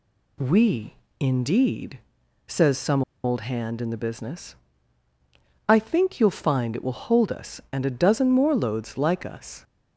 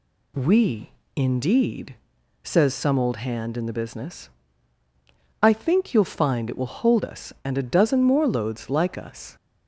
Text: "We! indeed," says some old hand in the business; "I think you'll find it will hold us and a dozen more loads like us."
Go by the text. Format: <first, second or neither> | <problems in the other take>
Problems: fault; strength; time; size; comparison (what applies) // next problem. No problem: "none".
second | pauses between "some" and "old"; slight; at 3.0 s; 0.21 s long